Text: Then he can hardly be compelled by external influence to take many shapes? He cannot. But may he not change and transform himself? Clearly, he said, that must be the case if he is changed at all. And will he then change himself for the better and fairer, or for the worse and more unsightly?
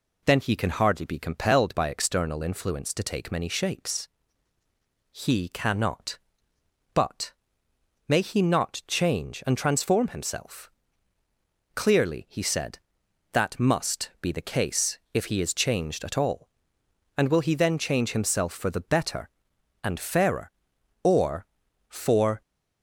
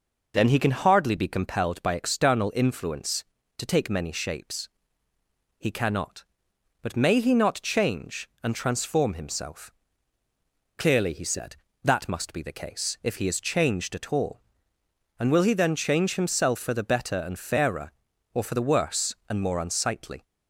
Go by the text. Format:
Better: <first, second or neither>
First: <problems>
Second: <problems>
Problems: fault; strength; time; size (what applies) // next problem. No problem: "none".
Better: second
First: pauses between "But" and "may"; noticeable; at 7.3 s; 0.76 s long // pauses between "case" and "if"; slight; at 14.9 s; 0.16 s long // stops before "the worse and more unsightly"; at 22.4 s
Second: none